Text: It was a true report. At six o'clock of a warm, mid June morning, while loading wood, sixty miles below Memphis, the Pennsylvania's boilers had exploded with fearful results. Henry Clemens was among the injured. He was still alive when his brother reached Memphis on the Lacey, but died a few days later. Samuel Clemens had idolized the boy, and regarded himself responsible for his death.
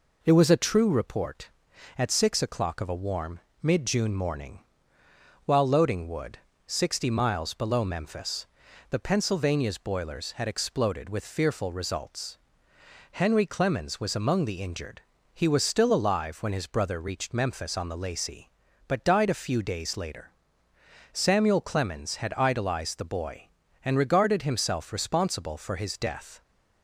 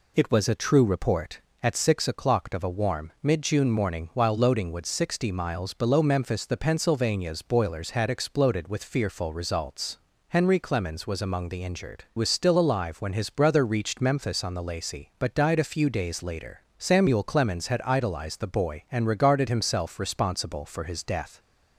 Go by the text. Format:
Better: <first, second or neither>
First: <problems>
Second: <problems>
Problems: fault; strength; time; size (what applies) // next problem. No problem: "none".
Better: first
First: none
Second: skips "He"; at 12.1 s